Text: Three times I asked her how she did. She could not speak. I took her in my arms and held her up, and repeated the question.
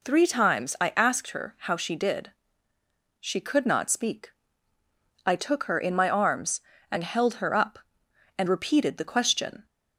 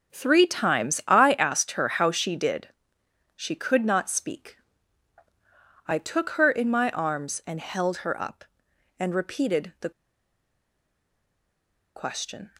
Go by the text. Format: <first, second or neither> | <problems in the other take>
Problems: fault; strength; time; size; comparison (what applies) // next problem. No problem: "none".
first | starts louder than the rest; until 1.1 s; 6 dB // pauses between "the" and "question"; strong; at 9.8 s; 2.0 s long